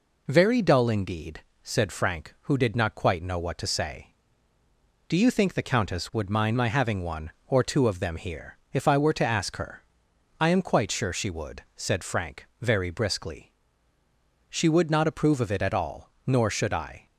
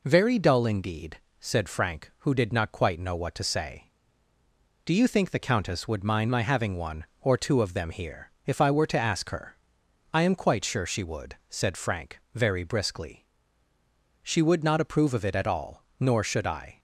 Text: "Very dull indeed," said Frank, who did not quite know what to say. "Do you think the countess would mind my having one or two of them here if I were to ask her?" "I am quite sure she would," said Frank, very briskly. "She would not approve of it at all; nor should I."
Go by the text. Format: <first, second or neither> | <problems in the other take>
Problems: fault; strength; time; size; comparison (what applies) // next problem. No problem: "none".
neither | pauses between "here" and "if"; slight; the same in both